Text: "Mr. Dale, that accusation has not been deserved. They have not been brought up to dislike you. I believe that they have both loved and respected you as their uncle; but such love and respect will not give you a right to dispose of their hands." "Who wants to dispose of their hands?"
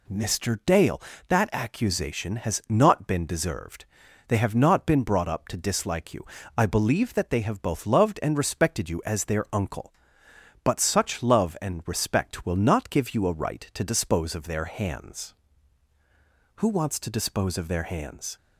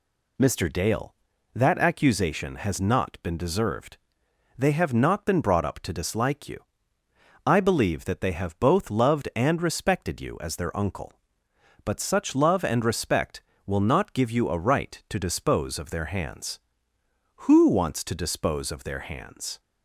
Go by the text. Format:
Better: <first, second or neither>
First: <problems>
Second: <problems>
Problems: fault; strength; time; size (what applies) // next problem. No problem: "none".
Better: neither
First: none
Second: none